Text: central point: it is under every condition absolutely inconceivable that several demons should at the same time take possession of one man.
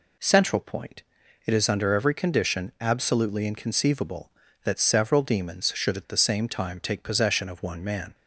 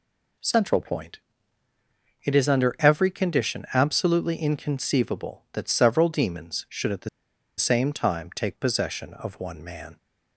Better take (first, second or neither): first